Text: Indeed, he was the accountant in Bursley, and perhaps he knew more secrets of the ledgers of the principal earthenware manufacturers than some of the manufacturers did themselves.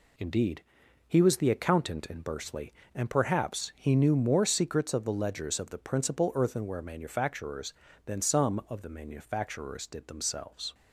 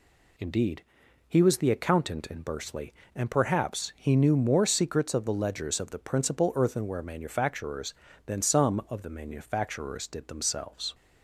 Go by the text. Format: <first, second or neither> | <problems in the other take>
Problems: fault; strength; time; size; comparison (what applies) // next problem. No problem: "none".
second | gets quieter; noticeable; throughout; 6 dB